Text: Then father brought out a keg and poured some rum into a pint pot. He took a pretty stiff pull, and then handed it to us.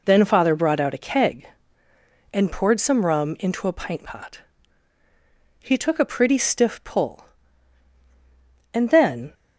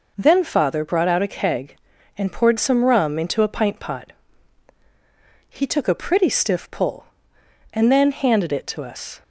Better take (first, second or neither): second